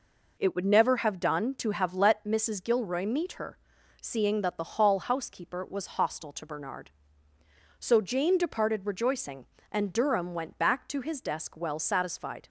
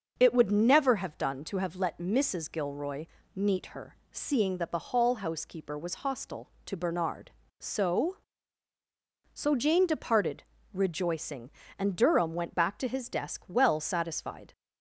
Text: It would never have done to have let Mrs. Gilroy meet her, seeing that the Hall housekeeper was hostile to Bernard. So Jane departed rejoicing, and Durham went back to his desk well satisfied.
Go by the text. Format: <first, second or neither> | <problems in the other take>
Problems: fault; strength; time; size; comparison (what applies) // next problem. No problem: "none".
first | starts louder than the rest; noticeable; until 1.1 s; 6 dB // pauses between "Gilroy" and "meet"; slight; at 3.0 s; 0.28 s long // says "So" twice; at 9.3 s // pauses between "departed" and "rejoicing"; slight; at 10.4 s; 0.28 s long